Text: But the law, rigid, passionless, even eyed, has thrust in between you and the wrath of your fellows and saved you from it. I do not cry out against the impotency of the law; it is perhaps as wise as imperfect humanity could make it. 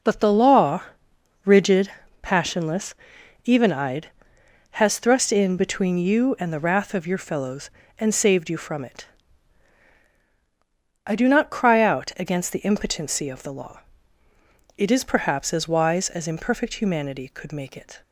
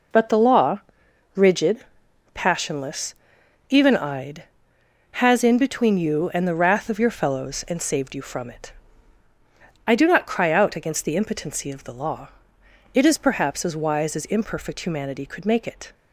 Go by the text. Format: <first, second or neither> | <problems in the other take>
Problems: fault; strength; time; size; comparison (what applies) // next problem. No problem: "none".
first | skips "thrust"; at 5.4 s